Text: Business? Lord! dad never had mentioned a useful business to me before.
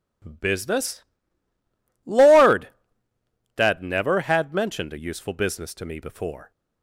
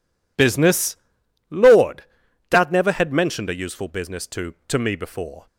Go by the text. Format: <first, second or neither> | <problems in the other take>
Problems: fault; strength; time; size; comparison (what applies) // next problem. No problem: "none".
first | says "to" twice; at 4.6 s